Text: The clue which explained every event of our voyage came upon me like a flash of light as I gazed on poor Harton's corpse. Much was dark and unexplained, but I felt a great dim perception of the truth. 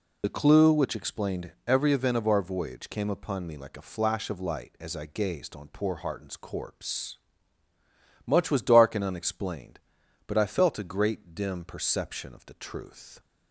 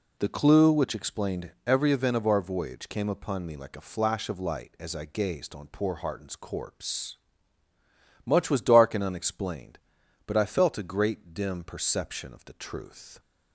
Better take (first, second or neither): second